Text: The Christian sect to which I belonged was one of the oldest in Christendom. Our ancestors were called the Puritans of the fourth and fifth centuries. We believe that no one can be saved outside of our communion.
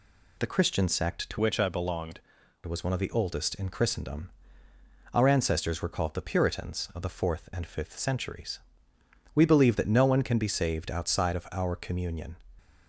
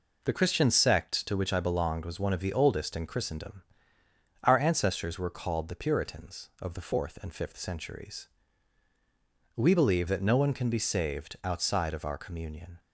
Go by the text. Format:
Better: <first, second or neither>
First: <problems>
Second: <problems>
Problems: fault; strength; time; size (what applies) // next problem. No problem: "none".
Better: second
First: changes voice from "which" to "belonged"; from 1.3 to 2.1 s; 0.8 s long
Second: none